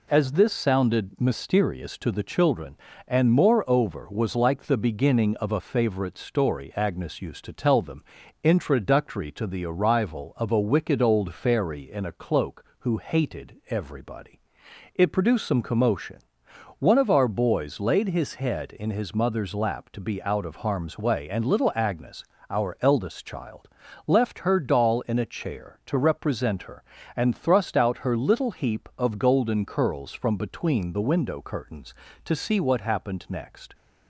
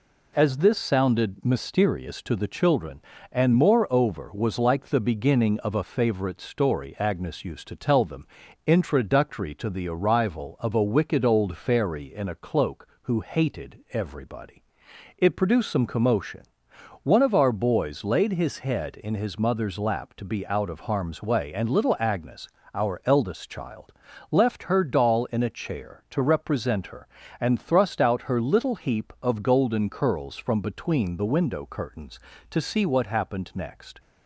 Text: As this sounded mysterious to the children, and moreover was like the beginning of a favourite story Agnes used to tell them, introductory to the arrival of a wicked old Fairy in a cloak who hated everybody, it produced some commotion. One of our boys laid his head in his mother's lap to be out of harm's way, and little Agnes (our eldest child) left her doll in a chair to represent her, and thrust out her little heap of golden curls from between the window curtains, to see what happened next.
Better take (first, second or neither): neither